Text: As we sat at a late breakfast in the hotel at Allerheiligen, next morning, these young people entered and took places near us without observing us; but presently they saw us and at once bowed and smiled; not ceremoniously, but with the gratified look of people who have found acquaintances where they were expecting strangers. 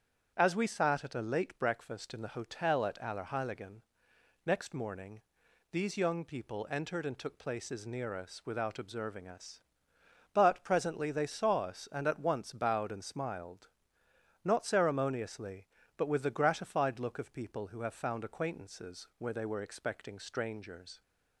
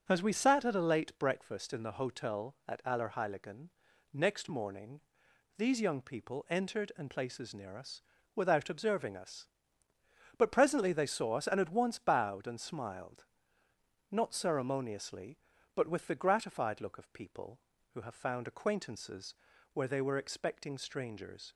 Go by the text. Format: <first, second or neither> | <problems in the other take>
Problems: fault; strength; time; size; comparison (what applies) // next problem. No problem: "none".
first | starts louder than the rest; until 1.0 s; 7 dB; strong in the first // skips "took"; at 7.1 s // pauses between "us" and "without"; slight; at 8.0 s; 0.34 s long // pauses between "acquaintances" and "where"; at 19.3 s; 0.38 s long